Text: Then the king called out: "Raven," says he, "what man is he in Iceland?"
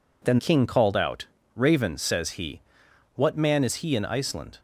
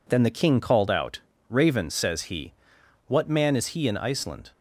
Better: second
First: skips "the"; at 0.3 s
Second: none

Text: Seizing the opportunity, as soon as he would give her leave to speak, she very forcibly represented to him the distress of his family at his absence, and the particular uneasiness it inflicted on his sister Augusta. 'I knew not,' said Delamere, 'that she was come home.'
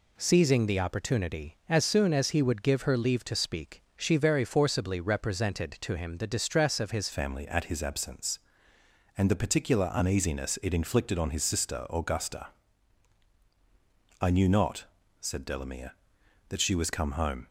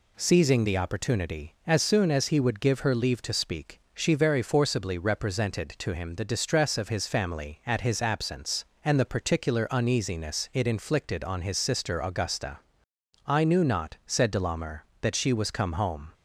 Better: second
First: changes voice at "family"; from 7.1 s on; 10.3 s long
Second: none

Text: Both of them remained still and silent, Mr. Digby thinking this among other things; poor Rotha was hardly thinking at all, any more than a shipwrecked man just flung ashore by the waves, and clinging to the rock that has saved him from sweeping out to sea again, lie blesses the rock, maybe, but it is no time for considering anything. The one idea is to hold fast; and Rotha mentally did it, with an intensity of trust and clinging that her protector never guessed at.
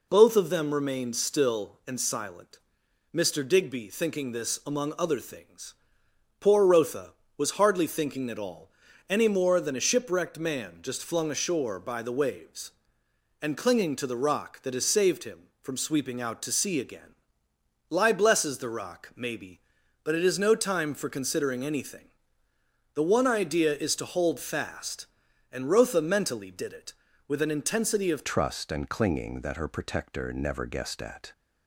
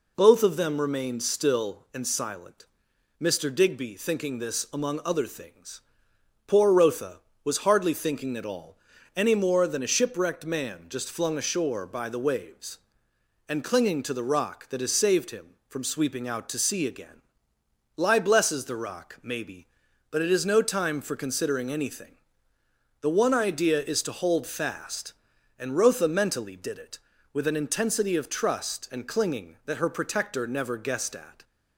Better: second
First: changes voice at "trust"; from 28.2 s on; 3.1 s long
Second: none

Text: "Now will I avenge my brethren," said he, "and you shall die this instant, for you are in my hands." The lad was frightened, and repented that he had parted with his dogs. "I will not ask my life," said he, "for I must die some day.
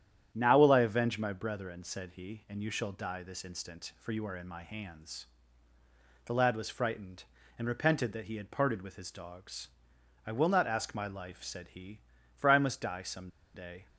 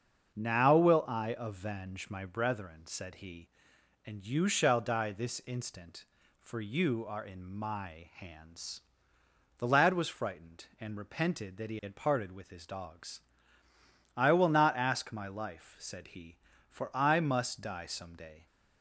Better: second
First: starts louder than the rest; strong; until 1.3 s; 9.5 dB // pauses between "some" and "day"; slight; at 13.2 s; 0.26 s long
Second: starts louder than the rest; until 1.3 s; 6.5 dB

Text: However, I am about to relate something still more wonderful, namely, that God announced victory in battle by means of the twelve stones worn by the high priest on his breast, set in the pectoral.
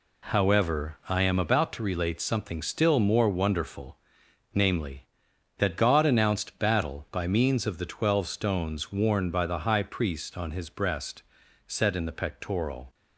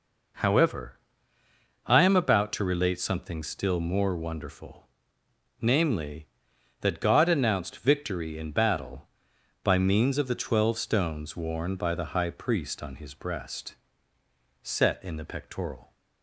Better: second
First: skips "victory in"; at 6.5 s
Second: none

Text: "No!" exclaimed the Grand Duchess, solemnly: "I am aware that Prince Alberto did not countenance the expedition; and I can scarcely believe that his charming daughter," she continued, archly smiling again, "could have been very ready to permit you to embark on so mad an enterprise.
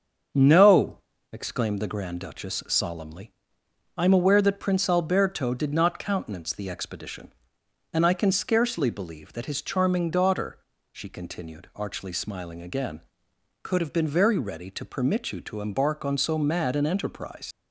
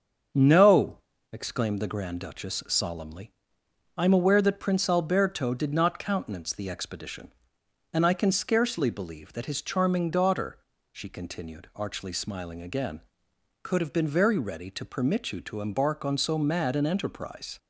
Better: second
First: starts louder than the rest; until 1.6 s; 7 dB // leaves "enterprise" unfinished; at 17.5 s; 65 ms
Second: starts louder than the rest; until 1.6 s; 7 dB

